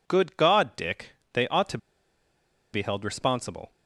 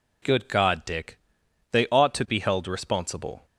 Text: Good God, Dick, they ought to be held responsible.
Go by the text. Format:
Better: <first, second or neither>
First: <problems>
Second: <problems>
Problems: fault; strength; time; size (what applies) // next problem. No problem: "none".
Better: second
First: pauses between "to" and "be"; noticeable; at 1.7 s; 0.94 s long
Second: none